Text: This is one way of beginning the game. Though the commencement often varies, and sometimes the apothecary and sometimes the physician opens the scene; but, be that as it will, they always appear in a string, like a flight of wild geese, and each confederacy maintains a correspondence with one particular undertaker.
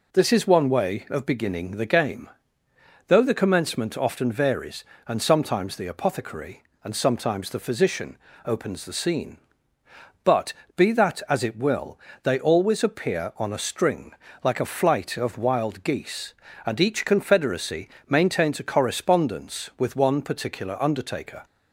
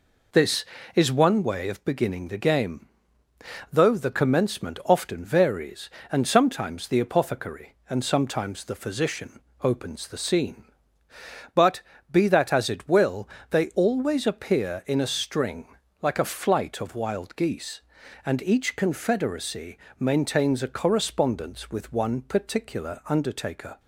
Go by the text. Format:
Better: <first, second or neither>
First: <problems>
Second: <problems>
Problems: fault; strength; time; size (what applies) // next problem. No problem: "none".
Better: second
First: pauses between "physician" and "opens"; slight; at 8.1 s; 0.26 s long // says "on" for "in"; at 13.3 s // pauses between "confederacy" and "maintains"; slight; at 17.8 s; 0.22 s long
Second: pauses between "physician" and "opens"; slight; at 9.3 s; 0.22 s long // pauses between "confederacy" and "maintains"; slight; at 19.7 s; 0.18 s long